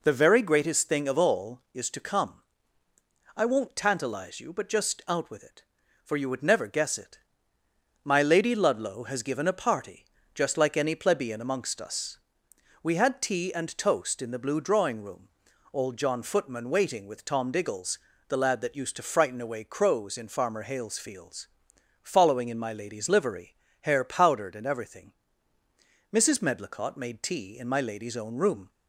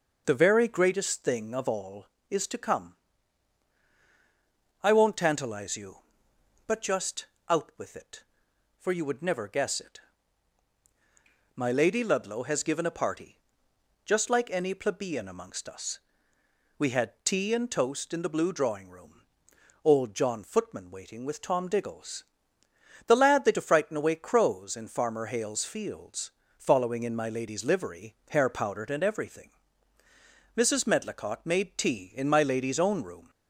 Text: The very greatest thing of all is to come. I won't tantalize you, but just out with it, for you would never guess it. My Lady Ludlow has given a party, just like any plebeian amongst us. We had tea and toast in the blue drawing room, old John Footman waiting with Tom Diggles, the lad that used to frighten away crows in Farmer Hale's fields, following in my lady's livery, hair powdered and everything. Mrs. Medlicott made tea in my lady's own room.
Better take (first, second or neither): first